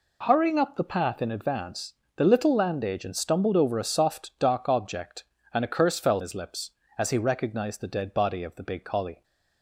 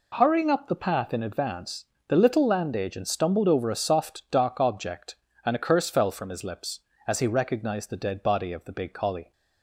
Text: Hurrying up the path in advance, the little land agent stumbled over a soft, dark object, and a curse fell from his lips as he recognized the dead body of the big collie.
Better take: second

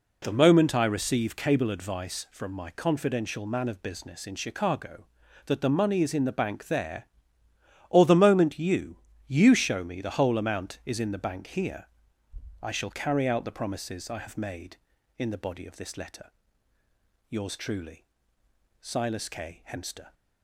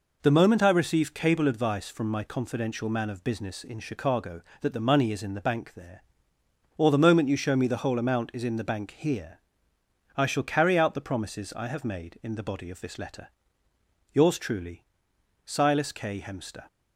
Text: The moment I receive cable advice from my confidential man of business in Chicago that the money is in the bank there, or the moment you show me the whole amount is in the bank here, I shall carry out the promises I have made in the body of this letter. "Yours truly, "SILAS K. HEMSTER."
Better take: second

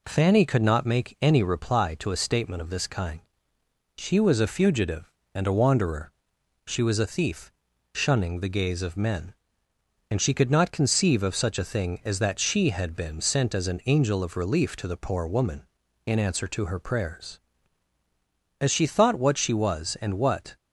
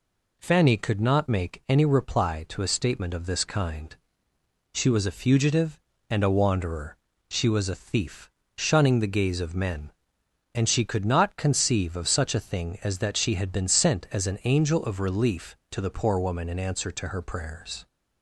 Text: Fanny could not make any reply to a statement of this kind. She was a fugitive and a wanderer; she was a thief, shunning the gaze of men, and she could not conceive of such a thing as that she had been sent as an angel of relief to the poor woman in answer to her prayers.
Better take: second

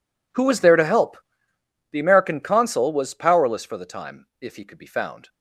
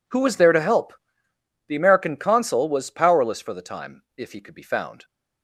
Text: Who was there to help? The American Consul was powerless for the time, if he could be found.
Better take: second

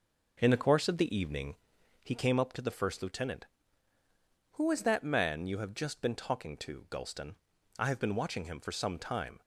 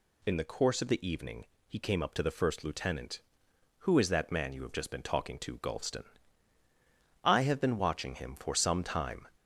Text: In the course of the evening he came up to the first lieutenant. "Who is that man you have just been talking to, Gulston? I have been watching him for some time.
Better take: second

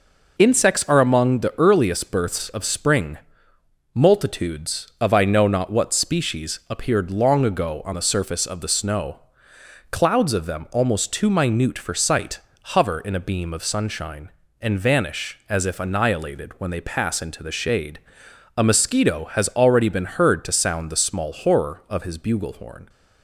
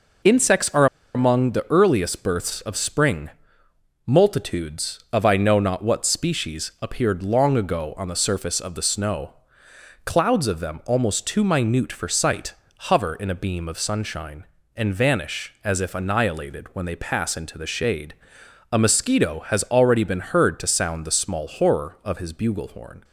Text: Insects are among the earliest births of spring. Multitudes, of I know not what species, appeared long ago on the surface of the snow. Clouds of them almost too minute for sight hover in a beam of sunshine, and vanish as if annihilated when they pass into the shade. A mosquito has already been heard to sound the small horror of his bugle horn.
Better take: first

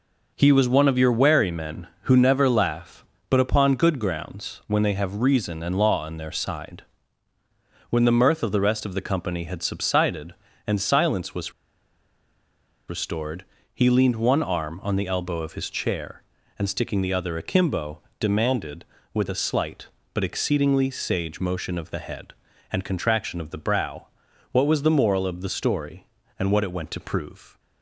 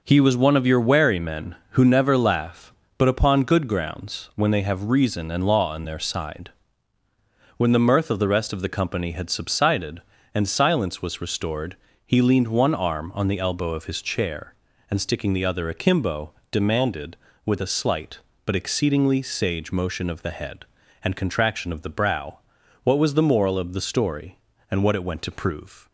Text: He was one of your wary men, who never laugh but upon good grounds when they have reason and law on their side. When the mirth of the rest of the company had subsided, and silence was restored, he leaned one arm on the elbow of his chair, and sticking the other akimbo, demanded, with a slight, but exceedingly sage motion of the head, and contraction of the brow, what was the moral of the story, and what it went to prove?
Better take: second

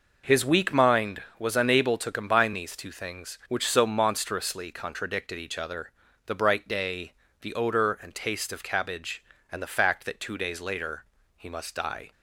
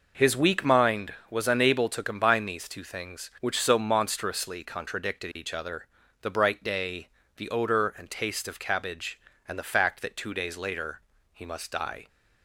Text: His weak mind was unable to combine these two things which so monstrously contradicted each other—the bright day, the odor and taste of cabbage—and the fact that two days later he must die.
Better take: neither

